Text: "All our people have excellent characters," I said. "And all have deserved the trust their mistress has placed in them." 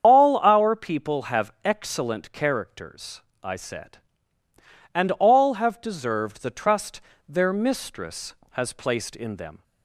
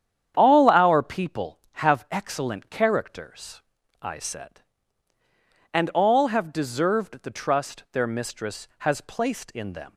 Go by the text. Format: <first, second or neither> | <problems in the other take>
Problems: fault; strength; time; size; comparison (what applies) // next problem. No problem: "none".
second | loses the start of "All"; at 0.0 s; 115 ms // starts louder than the rest; strong; until 1.0 s; 8 dB; strong in the second // pauses between "trust" and "their"; slight; at 7.0 s; 0.26 s long